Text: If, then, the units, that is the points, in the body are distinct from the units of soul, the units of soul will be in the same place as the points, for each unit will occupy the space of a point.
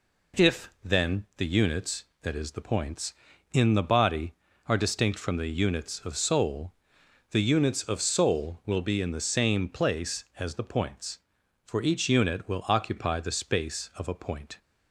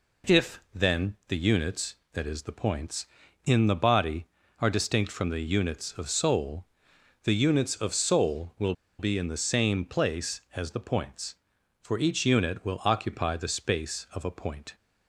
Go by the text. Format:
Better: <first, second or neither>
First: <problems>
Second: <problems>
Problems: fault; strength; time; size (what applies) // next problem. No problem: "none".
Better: first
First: none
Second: pauses between "will" and "be"; slight; at 8.7 s; 0.25 s long